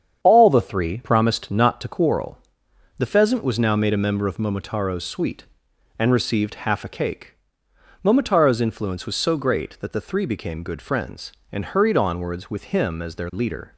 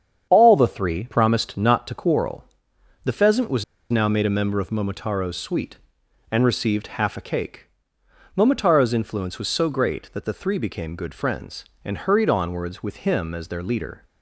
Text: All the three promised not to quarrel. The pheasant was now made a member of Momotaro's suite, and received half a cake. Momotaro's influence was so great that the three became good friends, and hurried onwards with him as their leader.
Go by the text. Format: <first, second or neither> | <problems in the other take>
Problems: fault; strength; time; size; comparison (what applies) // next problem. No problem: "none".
first | starts louder than the rest; strong; until 1.3 s; 8 dB; strong in the first // pauses between "was" and "now"; slight; at 3.6 s; 0.26 s long